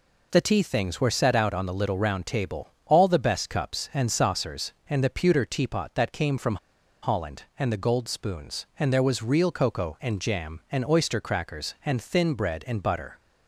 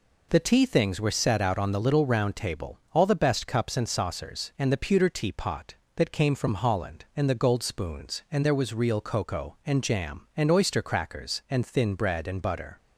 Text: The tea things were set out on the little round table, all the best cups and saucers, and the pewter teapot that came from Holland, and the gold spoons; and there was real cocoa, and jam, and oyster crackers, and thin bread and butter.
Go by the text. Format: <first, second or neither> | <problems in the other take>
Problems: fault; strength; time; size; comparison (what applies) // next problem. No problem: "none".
second | pauses between "from" and "Holland"; noticeable; at 6.5 s; 0.46 s long